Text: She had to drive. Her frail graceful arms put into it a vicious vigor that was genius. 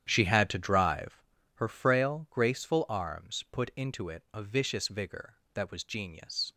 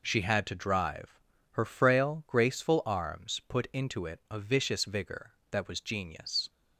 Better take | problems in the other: second | starts louder than the rest; strong; until 1.2 s; 9.5 dB

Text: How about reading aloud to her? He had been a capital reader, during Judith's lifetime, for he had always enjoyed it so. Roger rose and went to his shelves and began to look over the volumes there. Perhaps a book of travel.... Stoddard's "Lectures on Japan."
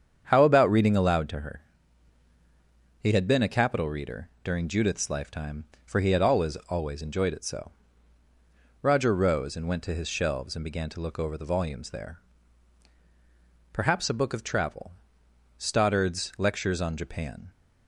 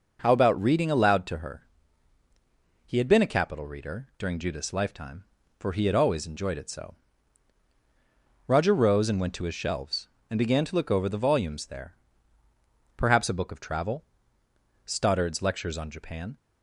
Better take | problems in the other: second | starts louder than the rest; strong; until 1.3 s; 8 dB // says "always" twice; at 6.6 s

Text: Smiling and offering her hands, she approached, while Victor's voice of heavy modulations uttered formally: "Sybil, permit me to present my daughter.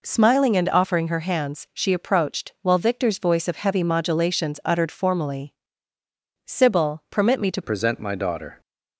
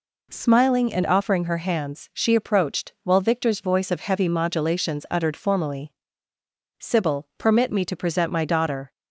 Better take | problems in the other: second | changes voice at "present"; from 7.6 s on; 1.0 s long

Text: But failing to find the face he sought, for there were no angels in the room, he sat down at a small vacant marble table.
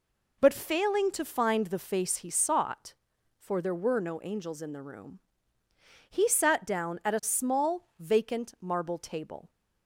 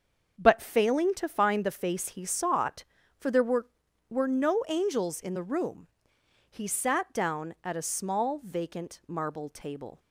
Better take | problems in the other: first | starts louder than the rest; until 1.3 s; 6.5 dB // says "were" twice; at 4.0 s

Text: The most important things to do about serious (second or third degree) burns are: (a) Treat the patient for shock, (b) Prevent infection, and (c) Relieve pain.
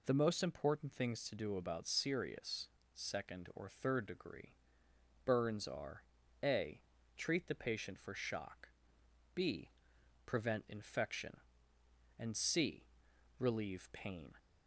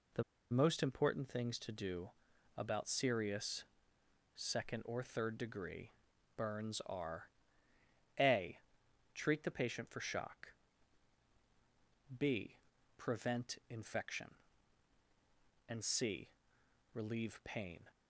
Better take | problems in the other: first | pauses between "The" and "most"; slight; at 0.2 s; 0.28 s long // pauses between "do" and "about"; noticeable; at 2.1 s; 0.46 s long

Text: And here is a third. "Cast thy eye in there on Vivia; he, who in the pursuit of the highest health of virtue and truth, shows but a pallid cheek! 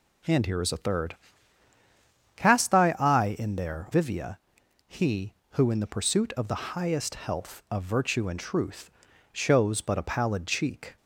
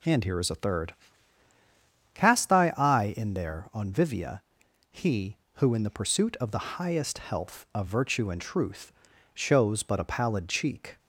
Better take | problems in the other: second | skips "on"; at 3.8 s

